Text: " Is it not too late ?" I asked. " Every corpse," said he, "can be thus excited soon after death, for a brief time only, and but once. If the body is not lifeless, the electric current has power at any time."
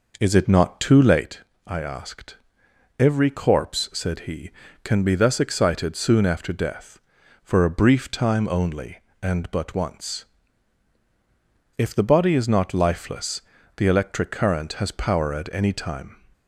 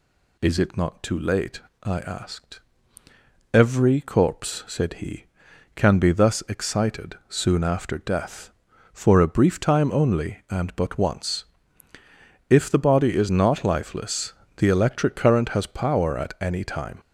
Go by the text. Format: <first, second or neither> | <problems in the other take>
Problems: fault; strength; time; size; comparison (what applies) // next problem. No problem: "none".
second | starts louder than the rest; noticeable; until 1.3 s; 5 dB